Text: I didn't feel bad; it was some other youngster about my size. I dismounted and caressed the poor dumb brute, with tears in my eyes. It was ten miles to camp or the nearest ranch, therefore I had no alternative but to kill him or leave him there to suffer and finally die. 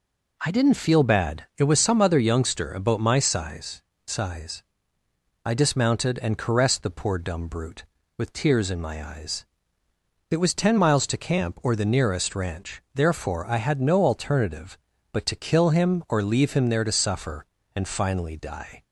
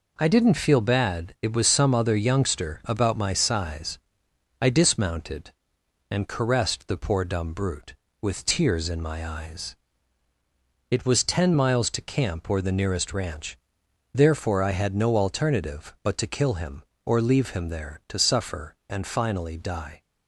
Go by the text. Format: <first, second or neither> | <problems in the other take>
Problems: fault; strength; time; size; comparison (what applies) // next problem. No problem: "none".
second | says "size" twice; at 4.0 s